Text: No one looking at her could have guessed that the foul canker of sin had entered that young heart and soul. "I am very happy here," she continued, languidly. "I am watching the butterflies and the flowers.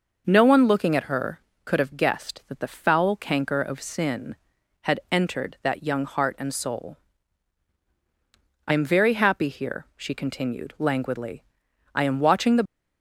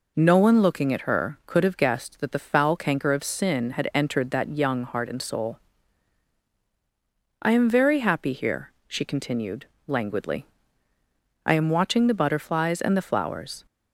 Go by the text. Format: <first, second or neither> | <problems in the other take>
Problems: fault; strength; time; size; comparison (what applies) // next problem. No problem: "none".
second | stops before "butterflies and the flowers"; at 12.6 s